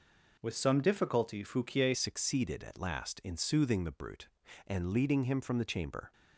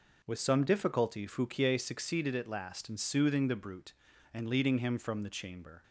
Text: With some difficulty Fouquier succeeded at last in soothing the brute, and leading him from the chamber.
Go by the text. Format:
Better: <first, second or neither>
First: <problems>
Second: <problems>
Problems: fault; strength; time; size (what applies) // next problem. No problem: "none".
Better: second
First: changes voice at "succeeded"; from 1.9 s on; 4.2 s long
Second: none